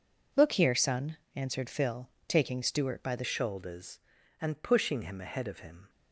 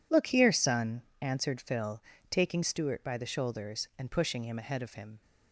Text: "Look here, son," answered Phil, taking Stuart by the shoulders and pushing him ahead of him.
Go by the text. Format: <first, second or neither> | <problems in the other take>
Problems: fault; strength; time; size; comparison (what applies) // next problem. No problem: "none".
second | changes voice at "shoulders"; from 3.2 s on; 2.6 s long